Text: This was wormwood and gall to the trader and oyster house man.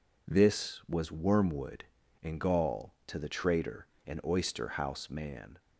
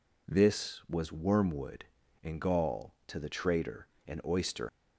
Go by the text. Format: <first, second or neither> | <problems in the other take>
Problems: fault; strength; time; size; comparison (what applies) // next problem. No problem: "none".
first | stops before "house man"; at 4.6 s